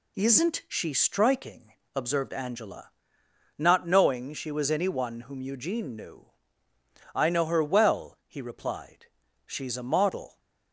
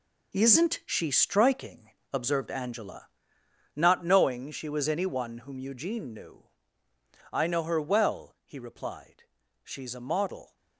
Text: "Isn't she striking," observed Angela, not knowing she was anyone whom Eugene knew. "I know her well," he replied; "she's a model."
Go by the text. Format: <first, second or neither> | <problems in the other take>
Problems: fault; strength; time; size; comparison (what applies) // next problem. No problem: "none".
first | gets quieter; strong; throughout; 11 dB